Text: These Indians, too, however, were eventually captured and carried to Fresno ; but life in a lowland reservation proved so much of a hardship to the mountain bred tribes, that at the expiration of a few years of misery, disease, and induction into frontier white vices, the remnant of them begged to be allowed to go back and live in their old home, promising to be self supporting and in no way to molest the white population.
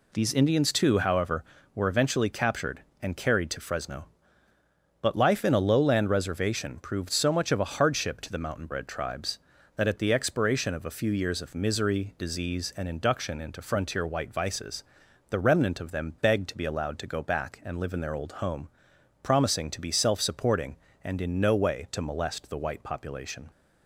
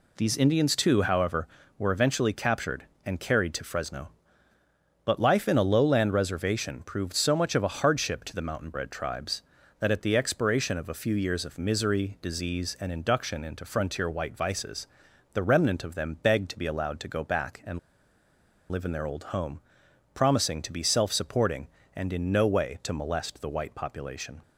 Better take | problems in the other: first | pauses between "and" and "live"; noticeable; at 17.7 s; 0.92 s long

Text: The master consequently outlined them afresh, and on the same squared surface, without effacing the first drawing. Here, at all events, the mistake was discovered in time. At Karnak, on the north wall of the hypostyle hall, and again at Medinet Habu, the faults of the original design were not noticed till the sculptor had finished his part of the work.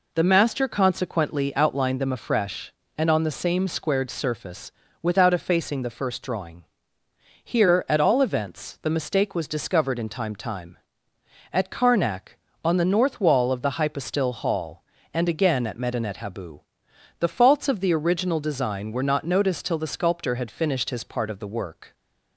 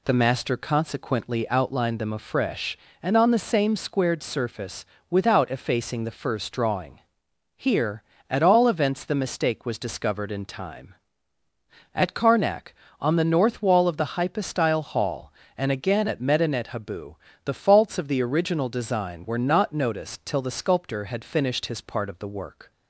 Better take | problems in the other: second | says "time" twice; at 10.3 s

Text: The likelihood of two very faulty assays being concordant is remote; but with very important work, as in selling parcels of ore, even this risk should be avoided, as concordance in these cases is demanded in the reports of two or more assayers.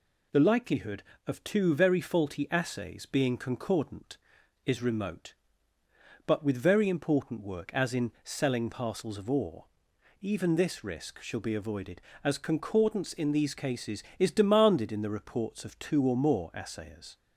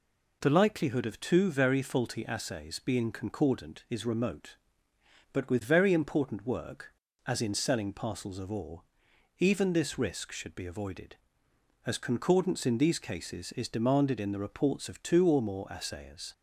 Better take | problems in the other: second | says "shall" for "should"; at 11.2 s

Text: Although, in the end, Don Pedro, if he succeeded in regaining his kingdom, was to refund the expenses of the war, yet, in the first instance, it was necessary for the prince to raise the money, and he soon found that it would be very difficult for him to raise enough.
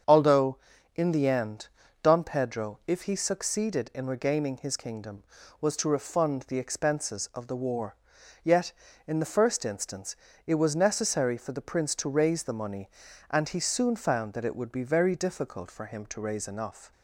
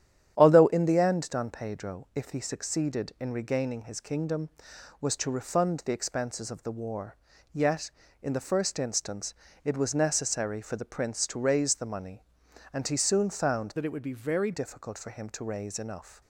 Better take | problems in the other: first | starts louder than the rest; strong; until 1.3 s; 10 dB; strong in the first // changes voice from "that" to "very"; from 13.7 to 14.5 s; 0.8 s long

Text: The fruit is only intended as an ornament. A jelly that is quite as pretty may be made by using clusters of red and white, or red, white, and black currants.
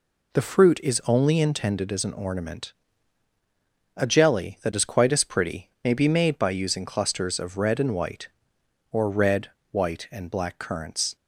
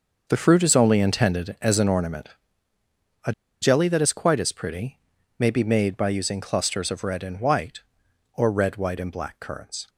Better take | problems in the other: first | starts louder than the rest; noticeable; until 1.2 s; 6 dB // pauses between "A" and "jelly"; slight; at 3.3 s; 0.30 s long // pauses between "pretty" and "may"; at 4.9 s; 0.38 s long

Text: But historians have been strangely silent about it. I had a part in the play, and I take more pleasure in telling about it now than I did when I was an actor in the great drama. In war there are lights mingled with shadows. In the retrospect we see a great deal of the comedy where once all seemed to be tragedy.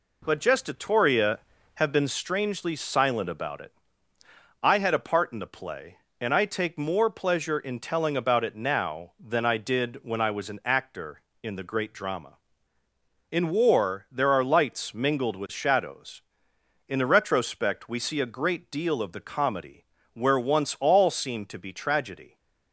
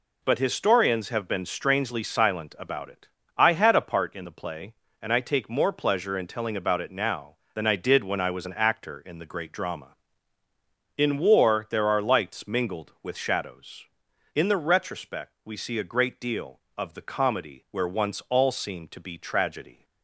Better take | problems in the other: second | says "gestatoria" for "historians"; at 0.3 s // pauses between "comedy" and "where"; slight; at 19.8 s; 0.30 s long

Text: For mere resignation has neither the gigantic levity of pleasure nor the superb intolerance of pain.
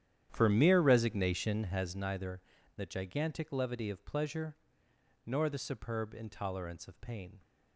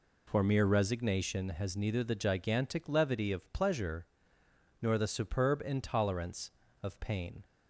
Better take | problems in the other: second | starts louder than the rest; strong; until 2.0 s; 10 dB // pauses between "neither" and "the"; slight; at 2.4 s; 0.36 s long // pauses between "pleasure" and "nor"; noticeable; at 4.5 s; 0.72 s long; noticeable in the second

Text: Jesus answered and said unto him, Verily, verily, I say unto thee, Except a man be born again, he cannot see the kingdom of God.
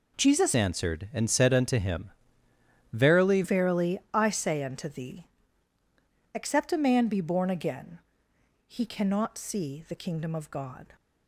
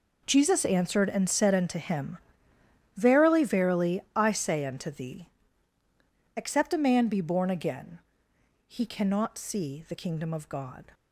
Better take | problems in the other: second | changes voice from "answered" to "Verily"; from 0.5 to 3.4 s; 2.9 s long

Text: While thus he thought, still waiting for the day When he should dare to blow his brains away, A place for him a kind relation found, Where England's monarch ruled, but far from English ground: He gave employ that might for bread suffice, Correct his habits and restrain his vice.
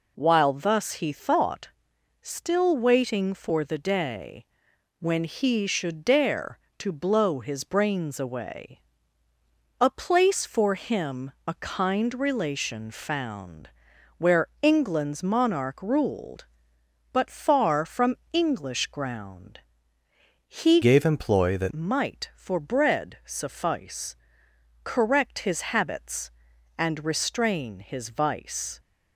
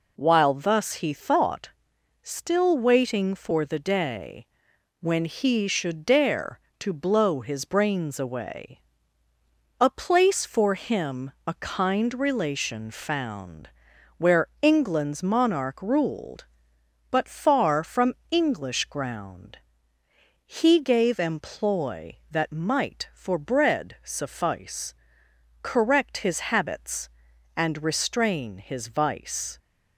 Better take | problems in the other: second | pauses between "day" and "When"; noticeable; at 4.4 s; 0.52 s long; noticeable in the second // pauses between "Where" and "England's"; slight; at 14.4 s; 0.16 s long; slight in the second // pauses between "from" and "English"; slight; at 18.1 s; 0.16 s long; slight in the second // changes voice from "gave" to "that"; from 20.8 to 21.7 s; 0.9 s long

